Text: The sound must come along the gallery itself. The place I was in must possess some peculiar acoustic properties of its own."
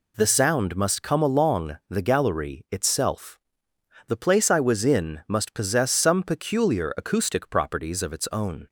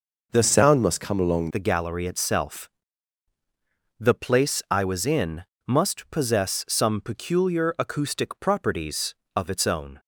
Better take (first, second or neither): first